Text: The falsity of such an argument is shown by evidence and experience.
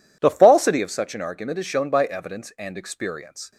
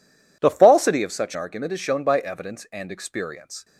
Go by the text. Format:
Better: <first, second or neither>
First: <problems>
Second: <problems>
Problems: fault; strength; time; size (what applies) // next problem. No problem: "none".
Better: first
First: none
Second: skips "an"; at 1.3 s